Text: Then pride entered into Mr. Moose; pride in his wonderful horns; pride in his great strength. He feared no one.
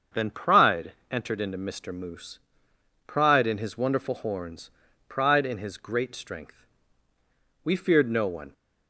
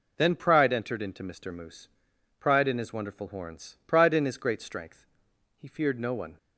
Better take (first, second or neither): second